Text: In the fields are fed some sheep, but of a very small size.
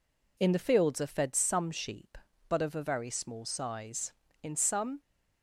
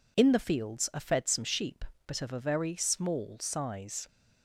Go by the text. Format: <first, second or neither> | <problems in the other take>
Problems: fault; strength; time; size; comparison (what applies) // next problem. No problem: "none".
second | goes on to say "In some"; from 4.4 s on; 0.58 s long